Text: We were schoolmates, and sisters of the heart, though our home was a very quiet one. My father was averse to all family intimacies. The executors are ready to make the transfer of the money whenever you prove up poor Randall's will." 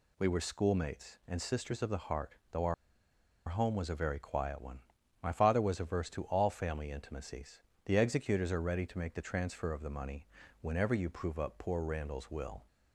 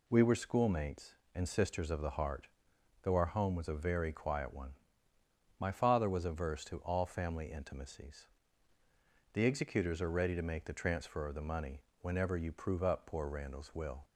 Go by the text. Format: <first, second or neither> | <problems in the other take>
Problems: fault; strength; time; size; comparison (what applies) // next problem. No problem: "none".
second | pauses between "our" and "home"; noticeable; at 2.7 s; 0.74 s long // pauses between "money" and "whenever"; slight; at 10.2 s; 0.32 s long; slight in the second